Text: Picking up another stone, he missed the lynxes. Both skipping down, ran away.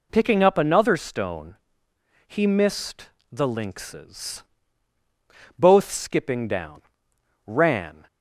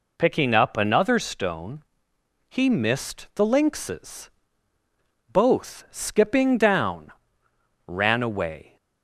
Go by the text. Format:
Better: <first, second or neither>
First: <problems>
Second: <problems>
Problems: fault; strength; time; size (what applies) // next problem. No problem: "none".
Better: second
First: pauses between "missed" and "the"; slight; at 3.1 s; 0.20 s long // stops before "away"; at 8.0 s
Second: none